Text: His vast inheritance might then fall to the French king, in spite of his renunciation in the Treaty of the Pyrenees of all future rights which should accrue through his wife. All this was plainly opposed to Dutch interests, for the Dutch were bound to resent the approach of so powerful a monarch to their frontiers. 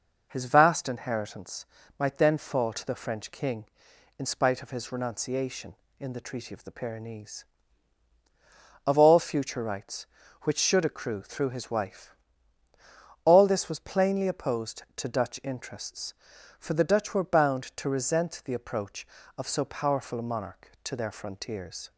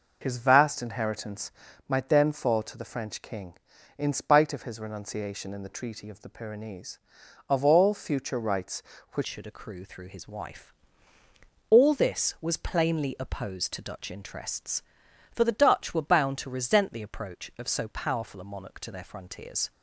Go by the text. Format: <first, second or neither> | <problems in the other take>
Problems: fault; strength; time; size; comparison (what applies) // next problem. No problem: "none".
first | pauses between "inheritance" and "might"; at 1.5 s; 0.38 s long; slight in the first // changes voice at "should"; from 9.2 s on; 10.5 s long